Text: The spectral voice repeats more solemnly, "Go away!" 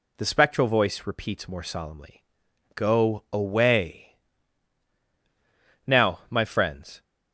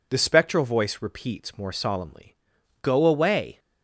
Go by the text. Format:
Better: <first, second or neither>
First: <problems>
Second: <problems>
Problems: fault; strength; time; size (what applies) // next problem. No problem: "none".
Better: second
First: goes on to say "Now my friends"; noticeable; from 5.8 s on; 1.1 s long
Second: none